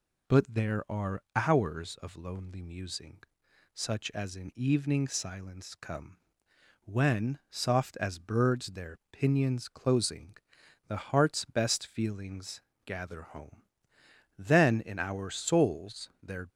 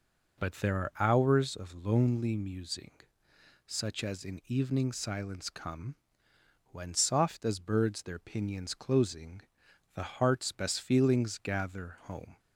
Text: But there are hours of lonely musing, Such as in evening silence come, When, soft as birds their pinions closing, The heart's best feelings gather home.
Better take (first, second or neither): second